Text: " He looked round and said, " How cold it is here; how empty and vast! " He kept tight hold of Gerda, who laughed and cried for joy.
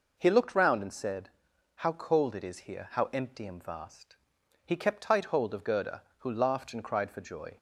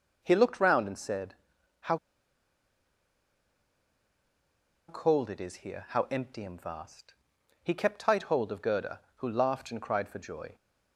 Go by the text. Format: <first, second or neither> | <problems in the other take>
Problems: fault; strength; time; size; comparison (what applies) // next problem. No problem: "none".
first | pauses between "How" and "cold"; strong; at 1.9 s; 2.9 s long